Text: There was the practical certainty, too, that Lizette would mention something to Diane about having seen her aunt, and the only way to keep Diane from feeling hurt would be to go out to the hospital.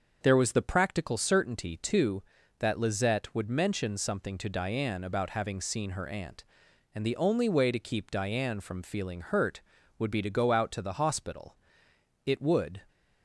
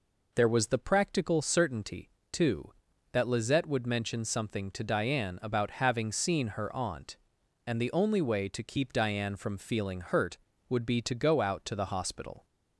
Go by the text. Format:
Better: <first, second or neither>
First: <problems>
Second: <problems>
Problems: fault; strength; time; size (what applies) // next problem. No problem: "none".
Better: second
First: starts louder than the rest; until 1.2 s; 6.5 dB // goes on to say "It would"; from 12.2 s on; 0.56 s long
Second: none